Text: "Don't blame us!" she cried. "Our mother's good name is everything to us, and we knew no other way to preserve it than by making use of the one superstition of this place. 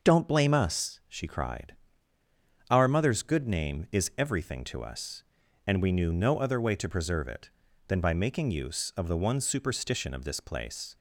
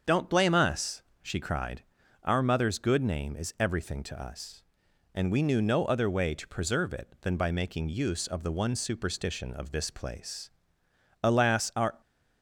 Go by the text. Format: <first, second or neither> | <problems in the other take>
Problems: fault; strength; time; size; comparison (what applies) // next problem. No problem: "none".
first | starts louder than the rest; until 1.2 s; 7 dB; noticeable in the first // goes on to say "Alas our"; noticeable; from 11.2 s on; 0.78 s long